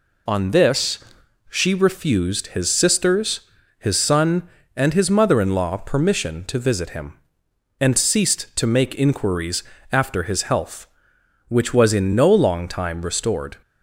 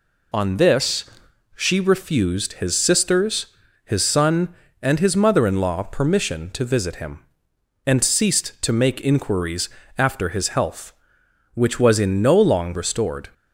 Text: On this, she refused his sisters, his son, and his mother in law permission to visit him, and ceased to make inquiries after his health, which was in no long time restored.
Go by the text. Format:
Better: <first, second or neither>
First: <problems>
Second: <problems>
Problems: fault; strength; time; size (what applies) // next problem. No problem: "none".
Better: first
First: pauses between "inquiries" and "after"; slight; at 9.6 s; 0.30 s long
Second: pauses between "inquiries" and "after"; slight; at 9.6 s; 0.30 s long // skips "time"; at 12.7 s